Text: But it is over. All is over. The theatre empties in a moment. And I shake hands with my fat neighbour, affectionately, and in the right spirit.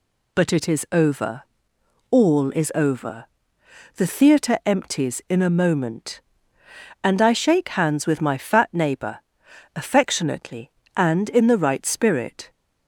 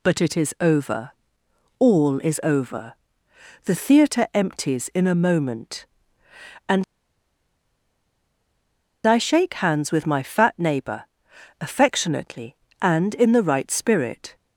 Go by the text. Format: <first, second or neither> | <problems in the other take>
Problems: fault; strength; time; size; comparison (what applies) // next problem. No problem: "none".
first | pauses between "And" and "I"; strong; at 6.8 s; 2.2 s long